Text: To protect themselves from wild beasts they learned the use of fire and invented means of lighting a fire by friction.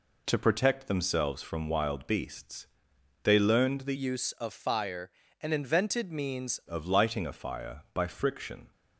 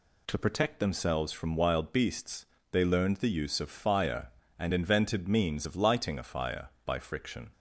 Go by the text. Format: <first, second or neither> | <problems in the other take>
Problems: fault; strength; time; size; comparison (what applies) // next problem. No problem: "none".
second | pauses between "beasts" and "they"; noticeable; at 2.6 s; 0.56 s long; slight in the second // changes voice from "use" to "means"; from 3.9 to 6.5 s; 2.6 s long